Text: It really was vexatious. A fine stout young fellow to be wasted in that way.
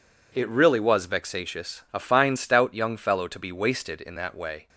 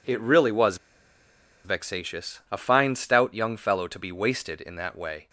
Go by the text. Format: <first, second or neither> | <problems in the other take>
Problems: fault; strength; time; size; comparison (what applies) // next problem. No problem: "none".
first | pauses between "was" and "vexatious"; noticeable; at 0.7 s; 0.87 s long